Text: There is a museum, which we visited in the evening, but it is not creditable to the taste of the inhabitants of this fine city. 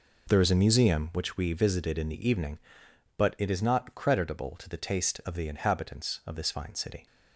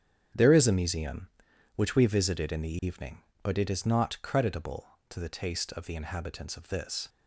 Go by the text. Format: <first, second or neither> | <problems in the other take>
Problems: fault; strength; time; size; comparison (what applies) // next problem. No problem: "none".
first | starts louder than the rest; strong; until 1.8 s; 9 dB // stops before "fine city"; at 7.0 s